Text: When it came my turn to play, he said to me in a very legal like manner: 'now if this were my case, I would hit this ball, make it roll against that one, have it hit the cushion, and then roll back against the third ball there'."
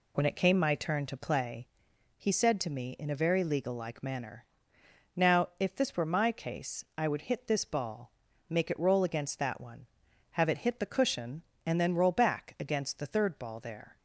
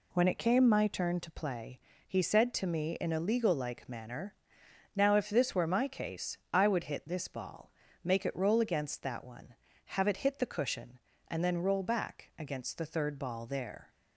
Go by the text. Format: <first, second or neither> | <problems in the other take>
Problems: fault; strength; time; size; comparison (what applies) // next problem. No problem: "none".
first | skips "very"; at 3.1 s